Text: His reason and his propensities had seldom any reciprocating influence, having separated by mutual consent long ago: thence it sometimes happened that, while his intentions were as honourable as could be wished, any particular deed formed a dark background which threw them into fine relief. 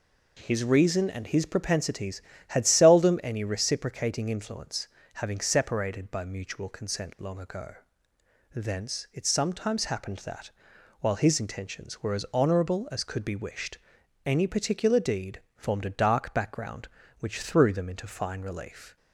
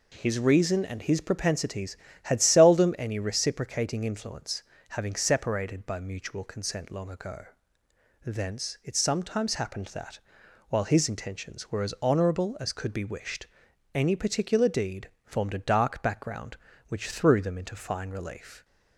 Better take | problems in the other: neither | pauses between "deed" and "formed"; slight; the same in both

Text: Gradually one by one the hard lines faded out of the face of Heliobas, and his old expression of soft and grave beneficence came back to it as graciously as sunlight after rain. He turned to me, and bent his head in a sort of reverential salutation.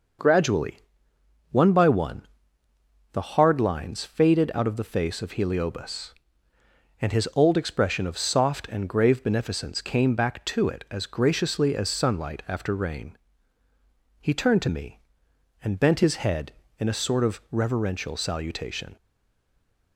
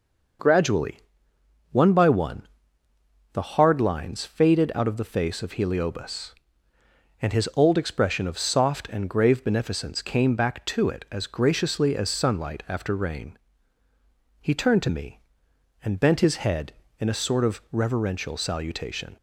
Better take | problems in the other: second | pauses between "Gradually" and "one"; noticeable; at 0.7 s; 0.70 s long; noticeable in the second // pauses between "one" and "the"; noticeable; at 2.2 s; 0.86 s long; noticeable in the second // stays silent after the last word; from 18.9 s on; 1.0 s long

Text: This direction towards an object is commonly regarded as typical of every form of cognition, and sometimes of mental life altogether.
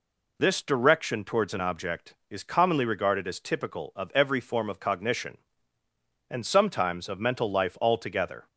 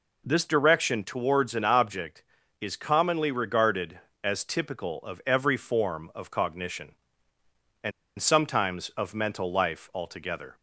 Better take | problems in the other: first | pauses between "and" and "sometimes"; slight; at 7.9 s; 0.28 s long

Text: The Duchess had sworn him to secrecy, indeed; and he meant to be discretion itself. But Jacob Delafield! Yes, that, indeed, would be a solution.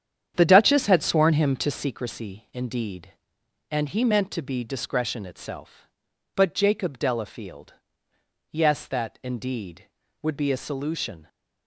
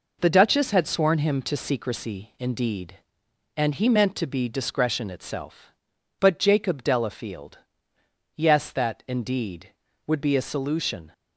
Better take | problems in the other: second | starts louder than the rest; strong; until 1.9 s; 9 dB

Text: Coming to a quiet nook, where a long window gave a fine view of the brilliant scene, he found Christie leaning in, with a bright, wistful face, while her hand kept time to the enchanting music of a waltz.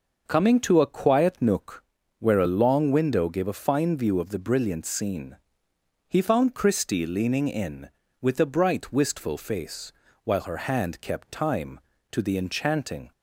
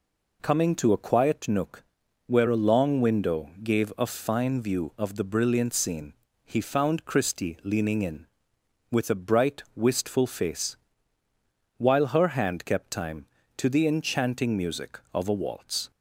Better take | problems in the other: second | stops before "music of a waltz"; at 13.1 s

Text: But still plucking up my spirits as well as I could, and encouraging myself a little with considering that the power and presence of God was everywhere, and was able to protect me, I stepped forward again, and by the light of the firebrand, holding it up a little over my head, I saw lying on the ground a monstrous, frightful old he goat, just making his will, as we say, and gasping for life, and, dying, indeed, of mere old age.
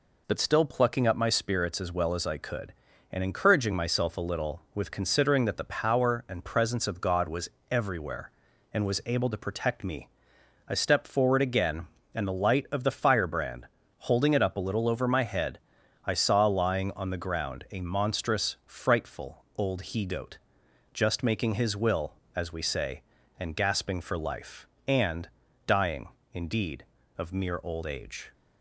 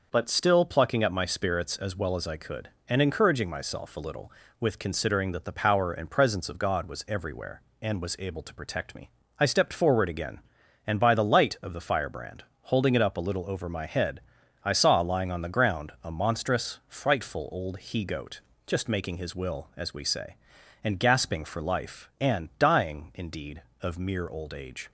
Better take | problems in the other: second | pauses between "was" and "everywhere"; slight; at 7.5 s; 0.20 s long // skips "by"; at 12.2 s

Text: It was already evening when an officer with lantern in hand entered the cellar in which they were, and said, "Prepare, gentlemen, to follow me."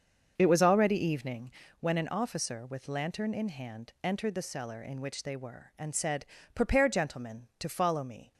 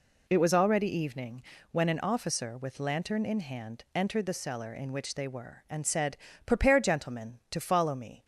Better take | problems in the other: second | starts louder than the rest; until 1.6 s; 6.5 dB // pauses between "evening" and "when"; slight; at 1.4 s; 0.30 s long; slight in the second

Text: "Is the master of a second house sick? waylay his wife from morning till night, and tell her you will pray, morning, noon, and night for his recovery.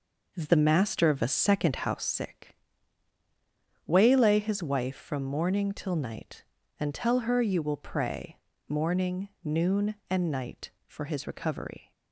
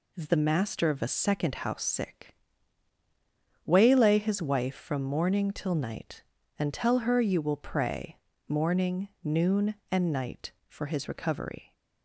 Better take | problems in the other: second | starts louder than the rest; noticeable; until 2.1 s; 5 dB

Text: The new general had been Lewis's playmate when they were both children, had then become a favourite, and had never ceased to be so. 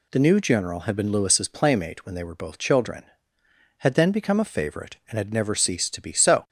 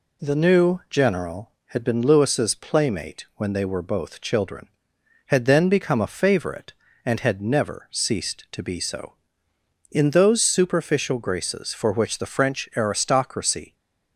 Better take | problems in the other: first | goes on to say "In those superficial graces for which the French aristocracy"; strong; from 9.9 s on; 3.8 s long

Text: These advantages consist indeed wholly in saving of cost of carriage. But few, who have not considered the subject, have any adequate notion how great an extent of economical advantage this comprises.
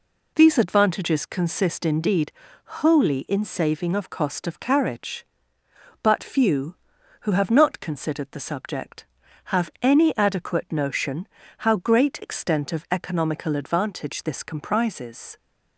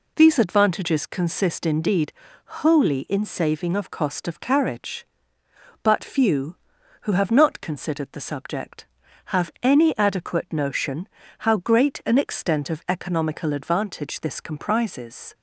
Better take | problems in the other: second | pauses between "indeed" and "wholly"; slight; at 2.3 s; 0.34 s long; slight in the second // pauses between "notion" and "how"; slight; at 11.2 s; 0.30 s long; slight in the second // skips "an"; at 12.2 s

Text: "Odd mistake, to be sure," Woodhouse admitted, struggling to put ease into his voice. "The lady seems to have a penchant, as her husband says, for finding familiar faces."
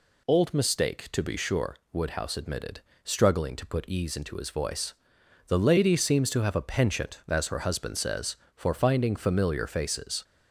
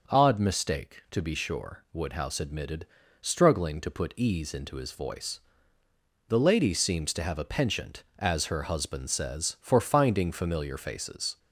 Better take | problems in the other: second | says "Old" for "Odd"; at 0.2 s

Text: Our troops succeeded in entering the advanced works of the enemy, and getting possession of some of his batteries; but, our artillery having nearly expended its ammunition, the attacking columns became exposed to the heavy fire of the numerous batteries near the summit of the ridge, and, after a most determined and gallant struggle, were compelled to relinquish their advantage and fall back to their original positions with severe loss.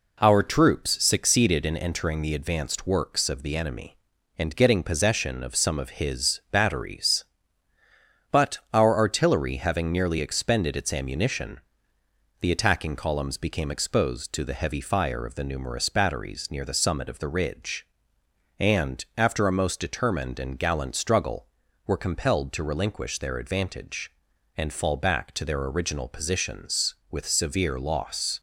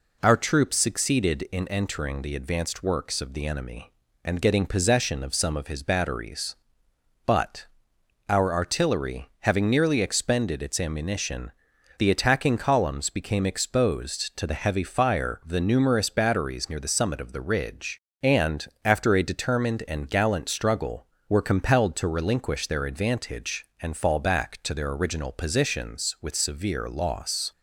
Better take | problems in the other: first | skips "most"; at 19.2 s

